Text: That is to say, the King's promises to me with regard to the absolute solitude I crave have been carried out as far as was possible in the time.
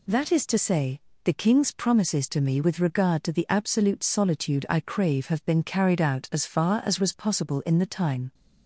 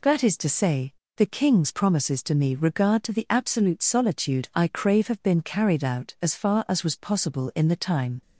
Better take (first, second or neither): first